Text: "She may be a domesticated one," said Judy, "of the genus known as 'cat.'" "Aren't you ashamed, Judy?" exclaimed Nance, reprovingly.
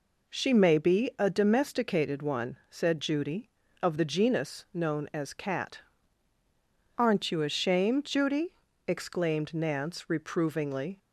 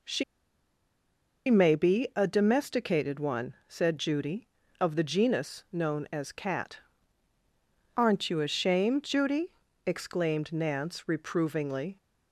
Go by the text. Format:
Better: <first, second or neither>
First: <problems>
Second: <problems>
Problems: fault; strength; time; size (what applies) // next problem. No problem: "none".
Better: first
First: none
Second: pauses between "She" and "may"; strong; at 0.2 s; 1.2 s long